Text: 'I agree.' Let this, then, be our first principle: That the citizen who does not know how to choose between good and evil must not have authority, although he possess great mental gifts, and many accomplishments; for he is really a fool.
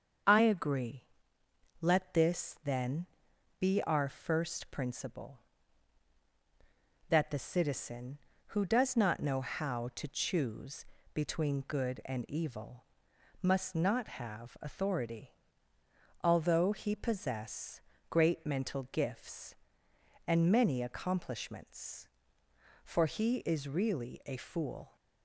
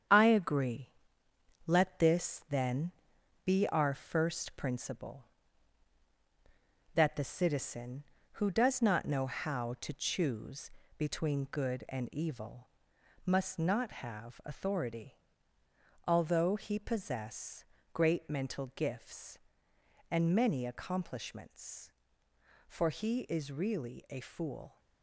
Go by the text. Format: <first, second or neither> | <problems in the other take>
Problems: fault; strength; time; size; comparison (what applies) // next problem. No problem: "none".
first | gets quieter; throughout; 7 dB // starts louder than the rest; strong; until 1.8 s; 8 dB; also in the first // pauses between "choose" and "between"; slight; at 10.6 s; 0.31 s long; slight in the first // pauses between "evil" and "must"; noticeable; at 12.6 s; 0.58 s long; noticeable in the first // pauses between "possess" and "great"; slight; at 17.6 s; 0.30 s long; slight in the first